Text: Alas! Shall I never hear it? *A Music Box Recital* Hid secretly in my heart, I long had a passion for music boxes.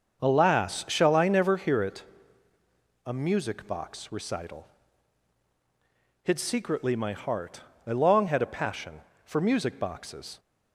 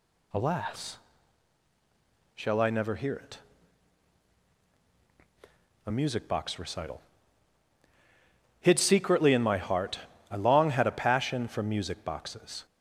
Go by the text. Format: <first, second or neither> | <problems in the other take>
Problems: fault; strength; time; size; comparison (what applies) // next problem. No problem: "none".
second | starts louder than the rest; until 1.2 s; 6.5 dB // pauses between "Recital" and "Hid"; strong; at 4.6 s; 1.5 s long; strong in the second // skips "in"; at 6.9 s